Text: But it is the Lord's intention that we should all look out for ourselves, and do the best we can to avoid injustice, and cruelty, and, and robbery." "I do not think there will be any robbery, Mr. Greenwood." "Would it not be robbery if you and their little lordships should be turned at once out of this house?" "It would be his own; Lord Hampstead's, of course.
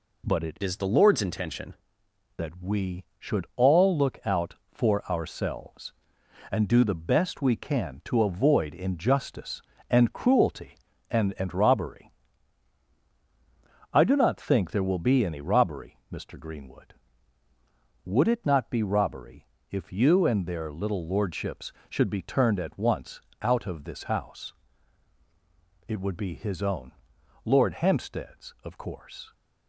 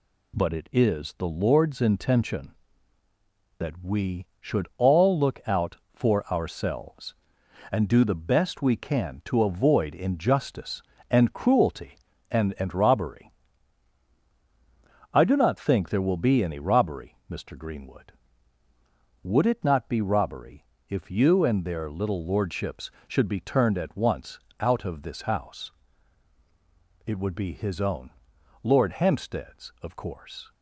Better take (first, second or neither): second